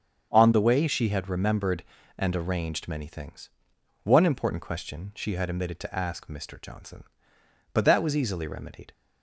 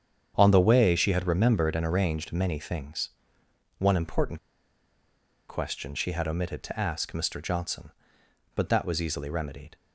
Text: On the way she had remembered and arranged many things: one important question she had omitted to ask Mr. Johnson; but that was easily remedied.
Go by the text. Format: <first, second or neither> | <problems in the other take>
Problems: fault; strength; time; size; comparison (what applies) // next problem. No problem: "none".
first | starts louder than the rest; strong; until 1.3 s; 8 dB; strong in the first // pauses between "important" and "question"; at 4.3 s; 1.1 s long